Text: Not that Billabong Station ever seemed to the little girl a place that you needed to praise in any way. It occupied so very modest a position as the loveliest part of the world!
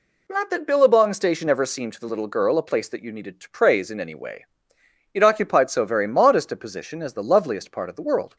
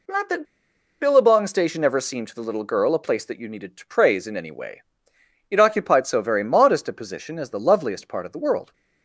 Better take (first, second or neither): first